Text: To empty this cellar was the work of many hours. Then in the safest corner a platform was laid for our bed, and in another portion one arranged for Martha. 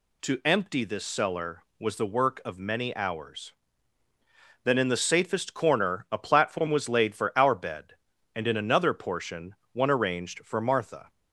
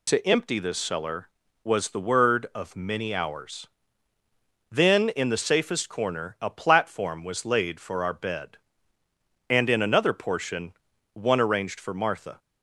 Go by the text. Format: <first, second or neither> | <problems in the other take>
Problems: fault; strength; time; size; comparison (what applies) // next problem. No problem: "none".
first | says "word" for "work"; at 2.0 s // pauses between "portion" and "one"; at 10.7 s; 0.40 s long; slight in the first